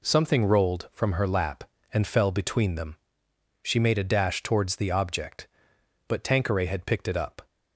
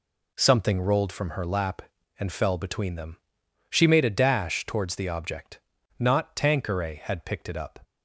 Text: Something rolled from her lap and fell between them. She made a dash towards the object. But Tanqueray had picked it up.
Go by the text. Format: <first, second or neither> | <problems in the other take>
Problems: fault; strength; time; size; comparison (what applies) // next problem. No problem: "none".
first | says "Not" for "But"; at 5.9 s